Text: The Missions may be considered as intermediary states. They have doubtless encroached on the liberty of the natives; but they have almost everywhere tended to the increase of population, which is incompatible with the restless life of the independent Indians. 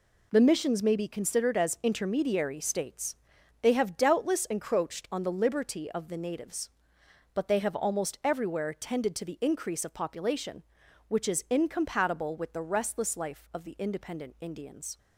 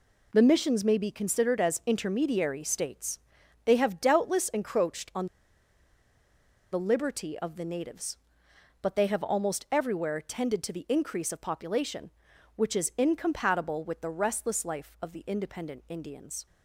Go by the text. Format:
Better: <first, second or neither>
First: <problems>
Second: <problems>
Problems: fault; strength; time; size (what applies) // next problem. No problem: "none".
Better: first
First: none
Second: pauses between "on" and "the"; strong; at 5.2 s; 1.4 s long